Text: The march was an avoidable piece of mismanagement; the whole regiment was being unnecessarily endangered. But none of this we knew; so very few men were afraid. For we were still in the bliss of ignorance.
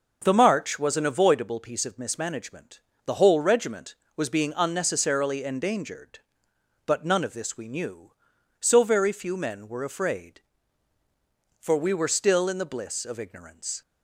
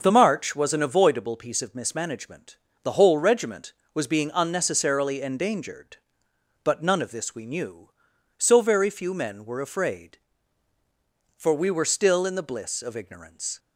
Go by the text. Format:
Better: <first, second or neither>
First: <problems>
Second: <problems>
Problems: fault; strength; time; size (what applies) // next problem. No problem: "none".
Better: neither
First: none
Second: none